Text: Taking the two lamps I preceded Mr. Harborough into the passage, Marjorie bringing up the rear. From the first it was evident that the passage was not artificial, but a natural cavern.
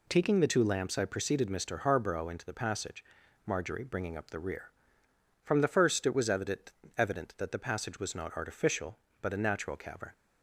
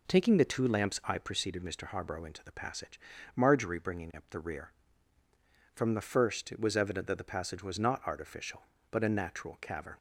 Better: second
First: says "evident" twice; at 6.9 s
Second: none

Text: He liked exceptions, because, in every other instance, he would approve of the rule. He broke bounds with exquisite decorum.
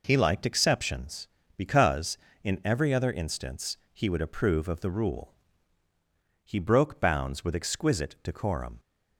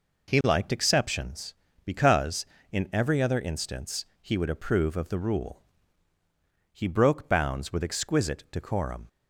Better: neither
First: none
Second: none

